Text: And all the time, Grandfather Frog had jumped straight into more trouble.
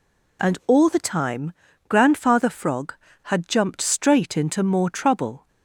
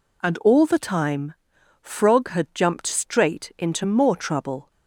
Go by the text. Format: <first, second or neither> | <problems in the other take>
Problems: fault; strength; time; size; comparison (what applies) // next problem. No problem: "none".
first | skips "Grandfather"; at 1.5 s